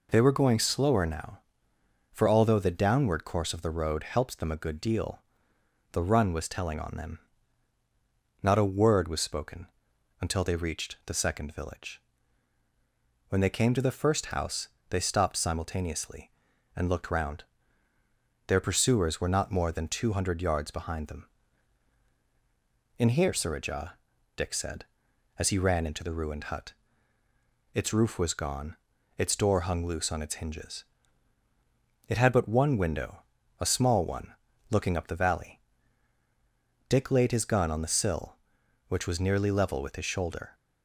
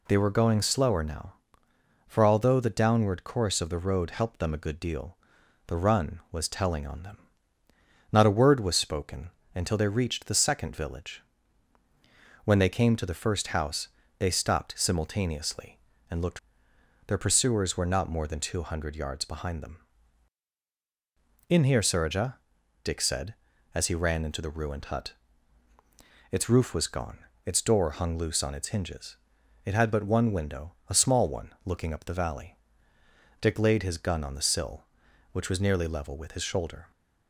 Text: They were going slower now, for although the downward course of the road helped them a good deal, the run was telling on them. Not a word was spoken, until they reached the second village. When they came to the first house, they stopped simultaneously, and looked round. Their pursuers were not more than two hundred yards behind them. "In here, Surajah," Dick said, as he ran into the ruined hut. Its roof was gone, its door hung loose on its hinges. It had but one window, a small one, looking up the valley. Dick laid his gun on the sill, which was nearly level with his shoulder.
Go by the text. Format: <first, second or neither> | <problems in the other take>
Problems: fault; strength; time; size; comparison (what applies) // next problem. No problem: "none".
first | skips "round"; at 16.7 s